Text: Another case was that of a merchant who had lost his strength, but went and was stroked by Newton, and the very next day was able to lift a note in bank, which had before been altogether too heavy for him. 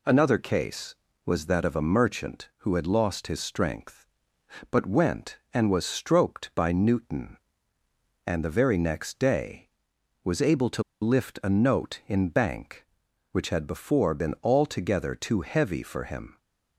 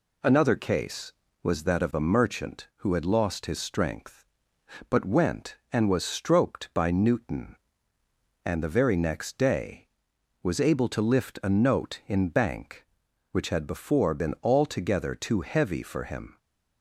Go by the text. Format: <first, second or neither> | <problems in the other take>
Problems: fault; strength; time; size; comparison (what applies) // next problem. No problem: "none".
second | pauses between "to" and "lift"; slight; at 10.8 s; 0.19 s long